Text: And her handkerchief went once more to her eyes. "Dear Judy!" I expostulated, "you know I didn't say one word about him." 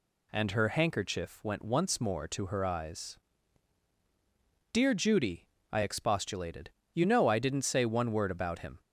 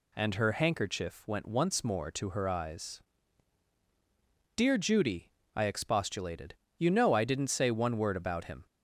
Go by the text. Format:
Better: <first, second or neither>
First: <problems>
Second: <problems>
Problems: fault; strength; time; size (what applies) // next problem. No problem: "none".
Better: neither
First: none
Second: none